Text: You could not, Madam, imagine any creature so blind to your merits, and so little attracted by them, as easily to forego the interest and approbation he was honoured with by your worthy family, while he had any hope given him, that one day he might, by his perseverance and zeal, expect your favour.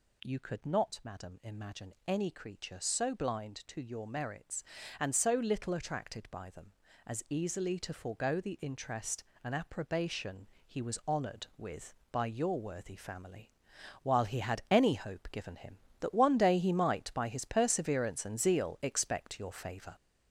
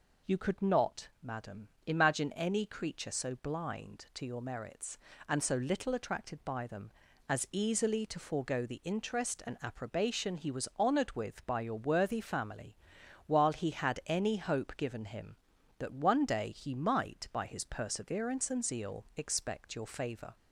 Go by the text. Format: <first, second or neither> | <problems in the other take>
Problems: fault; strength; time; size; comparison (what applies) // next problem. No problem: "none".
second | gets louder; noticeable; throughout; 6 dB // pauses between "approbation" and "he"; slight; at 10.4 s; 0.20 s long